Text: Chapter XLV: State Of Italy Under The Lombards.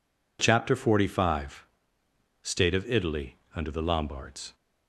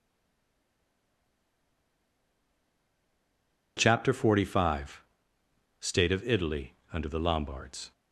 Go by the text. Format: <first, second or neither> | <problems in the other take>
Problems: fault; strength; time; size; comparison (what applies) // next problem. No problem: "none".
first | stays silent before the first word; strong; until 3.7 s; 3.7 s long // pauses between "Italy" and "Under"; slight; at 6.7 s; 0.18 s long; slight in the first